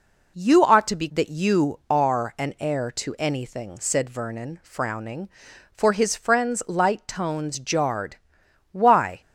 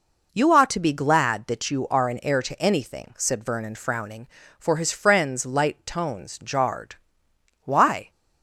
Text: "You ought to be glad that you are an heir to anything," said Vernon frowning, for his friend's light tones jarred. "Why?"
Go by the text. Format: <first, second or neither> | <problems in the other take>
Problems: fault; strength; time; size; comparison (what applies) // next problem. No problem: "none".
second | skips "glad"; at 1.0 s